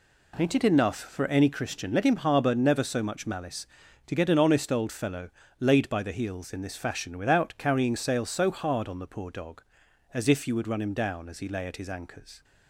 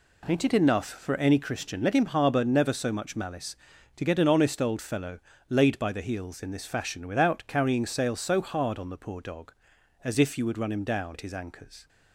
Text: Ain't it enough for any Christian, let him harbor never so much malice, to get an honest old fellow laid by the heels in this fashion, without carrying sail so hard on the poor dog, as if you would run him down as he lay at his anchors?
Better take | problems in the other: first | pauses between "fellow" and "laid"; slight; at 5.1 s; 0.32 s long; slight in the first // skips "as he lay"; at 11.1 s

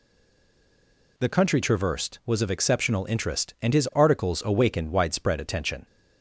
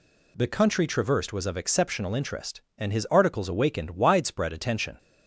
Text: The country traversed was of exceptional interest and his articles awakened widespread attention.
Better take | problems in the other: second | stays silent before the first word; noticeable; until 1.1 s; 1.1 s long

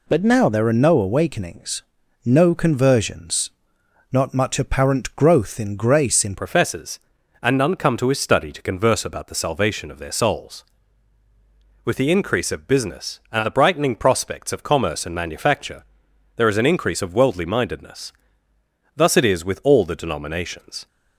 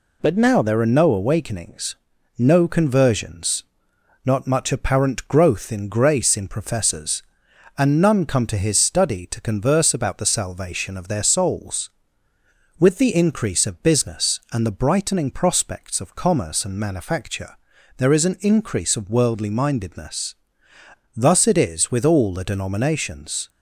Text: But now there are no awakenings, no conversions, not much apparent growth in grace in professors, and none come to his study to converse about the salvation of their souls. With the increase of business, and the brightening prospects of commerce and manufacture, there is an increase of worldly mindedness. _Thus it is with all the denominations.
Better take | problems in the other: second | changes voice at "professors"; from 6.3 s on; 14.5 s long

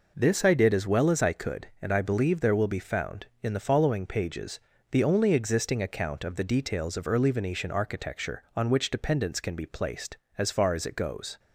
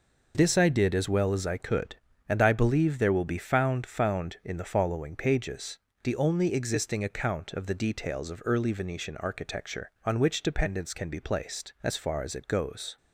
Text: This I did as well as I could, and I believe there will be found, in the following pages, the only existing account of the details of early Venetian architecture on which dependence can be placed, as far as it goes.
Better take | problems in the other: first | says "found" twice; at 3.8 s

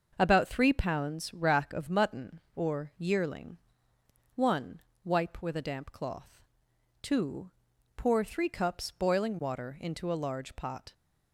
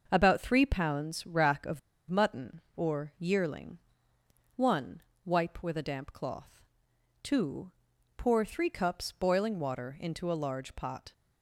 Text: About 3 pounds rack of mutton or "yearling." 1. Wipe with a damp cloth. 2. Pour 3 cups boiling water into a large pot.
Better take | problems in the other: first | starts louder than the rest; until 1.1 s; 6 dB; also in the first // pauses between "of" and "mutton"; slight; at 1.7 s; 0.30 s long

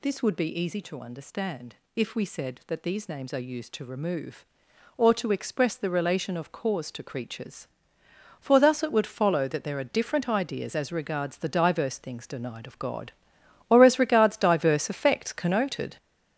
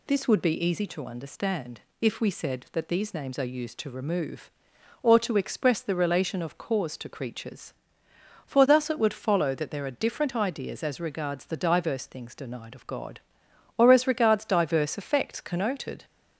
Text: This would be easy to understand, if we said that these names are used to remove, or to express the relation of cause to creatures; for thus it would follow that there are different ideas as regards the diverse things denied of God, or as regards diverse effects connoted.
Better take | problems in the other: second | gets louder; throughout; 7 dB

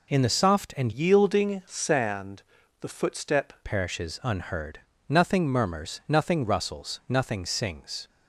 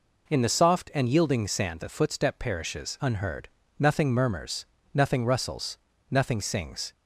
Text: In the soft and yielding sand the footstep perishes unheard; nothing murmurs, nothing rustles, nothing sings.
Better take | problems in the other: second | changes voice from "yielding" to "footstep"; from 0.9 to 3.5 s; 2.6 s long // pauses between "sand" and "the"; slight; at 2.4 s; 0.36 s long

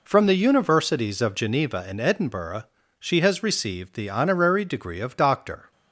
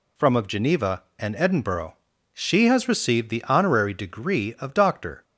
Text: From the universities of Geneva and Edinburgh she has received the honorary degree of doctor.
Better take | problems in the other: first | skips "the universities"; at 0.3 s // pauses between "Edinburgh" and "she"; at 1.9 s; 0.38 s long; slight in the first

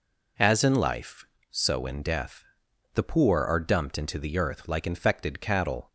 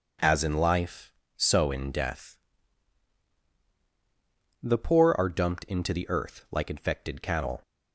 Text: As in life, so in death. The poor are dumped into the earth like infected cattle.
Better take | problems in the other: neither | none

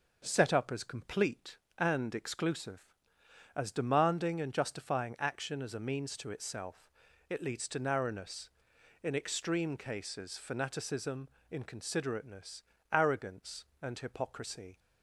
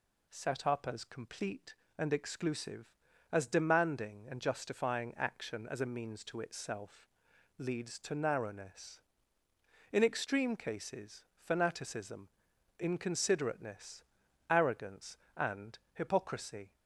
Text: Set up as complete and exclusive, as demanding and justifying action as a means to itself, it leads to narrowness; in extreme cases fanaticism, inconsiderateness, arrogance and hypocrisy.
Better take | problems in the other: first | skips "it"; at 7.3 s // pauses between "and" and "hypocrisy"; slight; at 15.7 s; 0.16 s long

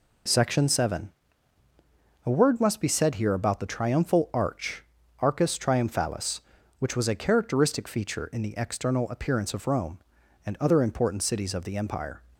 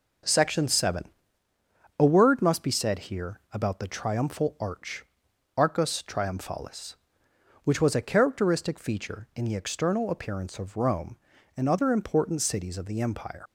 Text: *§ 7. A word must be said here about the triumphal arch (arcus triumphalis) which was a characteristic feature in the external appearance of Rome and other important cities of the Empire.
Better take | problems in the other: first | leaves "Empire" unfinished; at 13.4 s; 85 ms

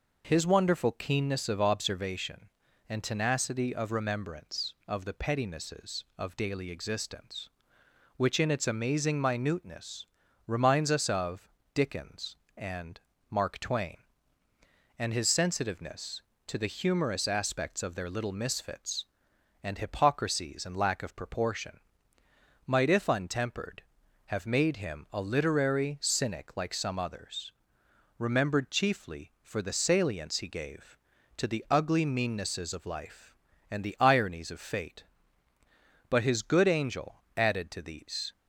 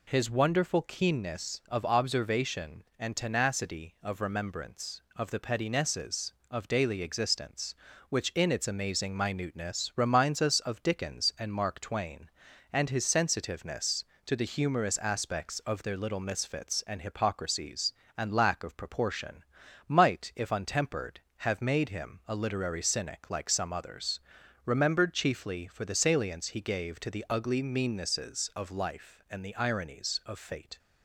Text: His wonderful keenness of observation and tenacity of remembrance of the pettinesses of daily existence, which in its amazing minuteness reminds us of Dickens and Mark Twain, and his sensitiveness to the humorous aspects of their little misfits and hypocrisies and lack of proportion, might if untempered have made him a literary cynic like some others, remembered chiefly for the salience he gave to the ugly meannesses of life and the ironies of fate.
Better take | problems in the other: second | pauses between "minuteness" and "reminds"; at 10.0 s; 0.44 s long // pauses between "of" and "Dickens"; slight; at 11.4 s; 0.28 s long // pauses between "and" and "Mark"; slight; at 12.9 s; 0.30 s long // goes on to say "But his good angel added to these"; strong; from 36.0 s on; 2.2 s long

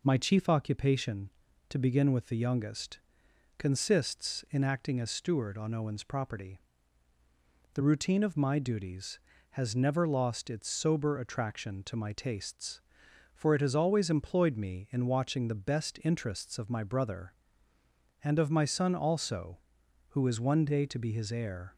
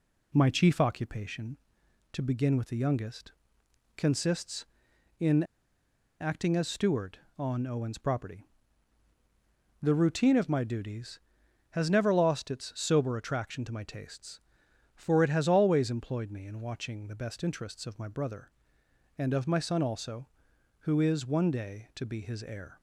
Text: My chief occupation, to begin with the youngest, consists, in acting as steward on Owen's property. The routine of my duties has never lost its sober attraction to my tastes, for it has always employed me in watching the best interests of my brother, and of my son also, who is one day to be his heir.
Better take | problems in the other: first | pauses between "in" and "acting"; noticeable; at 5.4 s; 0.77 s long

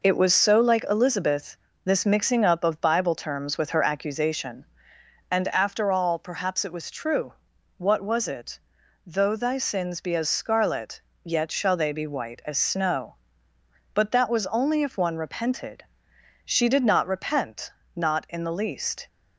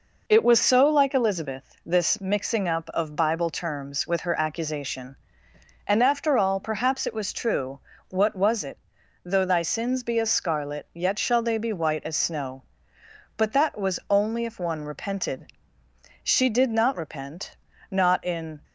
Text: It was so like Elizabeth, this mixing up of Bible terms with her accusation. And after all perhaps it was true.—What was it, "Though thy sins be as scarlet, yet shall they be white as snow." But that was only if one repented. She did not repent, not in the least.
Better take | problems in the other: first | stops before "the least"; at 18.6 s

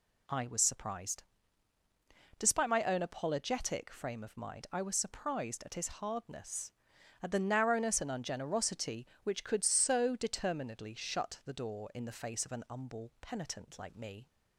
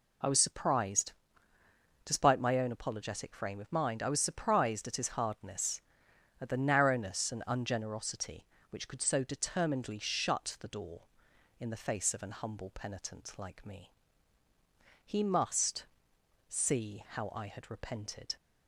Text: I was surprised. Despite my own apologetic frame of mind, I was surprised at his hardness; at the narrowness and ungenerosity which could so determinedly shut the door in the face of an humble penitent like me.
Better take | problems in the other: first | goes on to say "He must see how I had repented"; strong; from 15.0 s on; 3.3 s long

